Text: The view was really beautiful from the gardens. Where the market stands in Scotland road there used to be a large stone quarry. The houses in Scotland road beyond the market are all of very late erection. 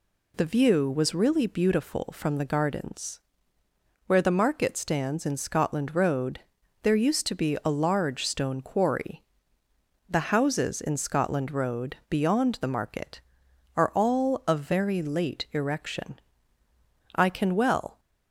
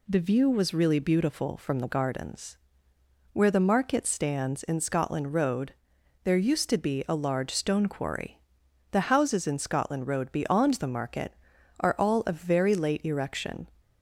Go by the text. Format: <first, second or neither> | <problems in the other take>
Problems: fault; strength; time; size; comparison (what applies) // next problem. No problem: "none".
second | pauses between "road" and "there"; at 6.3 s; 0.44 s long; noticeable in the second // pauses between "road" and "beyond"; slight; at 11.9 s; 0.16 s long // goes on to say "I can well"; noticeable; from 17.1 s on; 0.84 s long